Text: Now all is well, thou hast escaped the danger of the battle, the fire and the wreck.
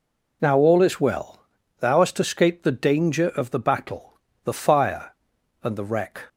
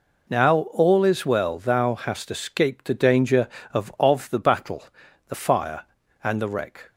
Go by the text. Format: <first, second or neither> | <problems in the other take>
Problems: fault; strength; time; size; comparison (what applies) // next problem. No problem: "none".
first | says "of" twice; at 3.9 s